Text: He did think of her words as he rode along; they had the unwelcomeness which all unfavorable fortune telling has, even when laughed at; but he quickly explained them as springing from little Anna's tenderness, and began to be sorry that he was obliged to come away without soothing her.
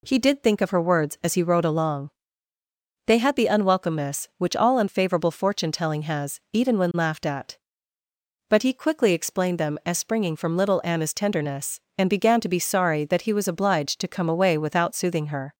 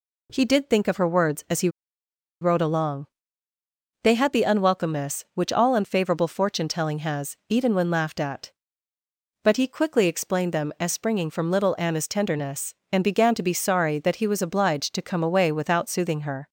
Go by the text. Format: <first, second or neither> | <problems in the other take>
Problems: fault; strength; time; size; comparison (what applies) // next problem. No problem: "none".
first | pauses between "he" and "rode"; noticeable; at 1.6 s; 0.72 s long